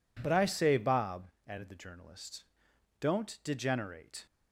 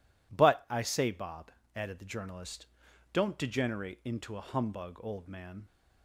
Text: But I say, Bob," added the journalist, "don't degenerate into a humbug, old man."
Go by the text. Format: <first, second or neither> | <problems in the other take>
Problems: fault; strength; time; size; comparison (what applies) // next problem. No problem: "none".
second | stops before "into a humbug old man"; at 4.2 s